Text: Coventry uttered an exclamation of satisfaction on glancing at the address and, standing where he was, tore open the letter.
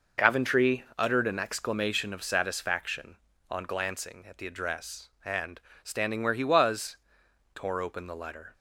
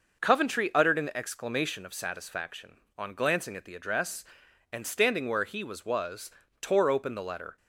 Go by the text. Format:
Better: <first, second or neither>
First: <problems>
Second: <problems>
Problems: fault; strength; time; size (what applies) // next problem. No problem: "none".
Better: first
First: none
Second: says "was" twice; at 5.8 s